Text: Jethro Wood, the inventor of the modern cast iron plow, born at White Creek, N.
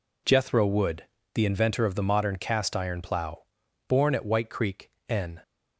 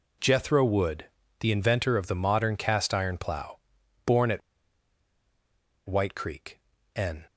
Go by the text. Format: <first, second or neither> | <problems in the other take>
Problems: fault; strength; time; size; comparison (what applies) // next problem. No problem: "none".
first | pauses between "at" and "White"; strong; at 4.4 s; 1.4 s long